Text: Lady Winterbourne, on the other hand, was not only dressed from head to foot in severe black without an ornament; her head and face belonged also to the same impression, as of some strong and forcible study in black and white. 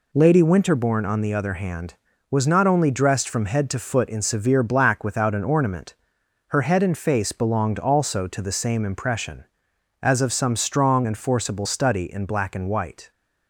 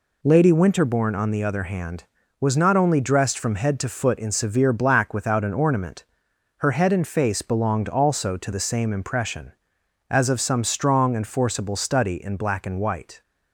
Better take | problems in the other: neither | none

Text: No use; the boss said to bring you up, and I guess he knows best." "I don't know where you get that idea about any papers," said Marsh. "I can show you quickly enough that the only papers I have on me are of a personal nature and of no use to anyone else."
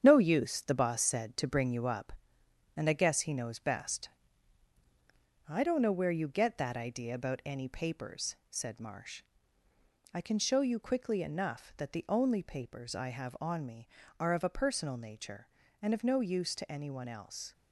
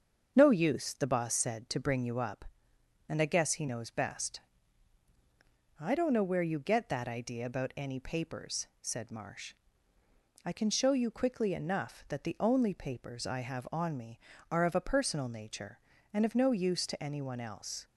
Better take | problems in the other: second | gets quieter; throughout; 6.5 dB // starts louder than the rest; strong; until 1.0 s; 8.5 dB; also in the second

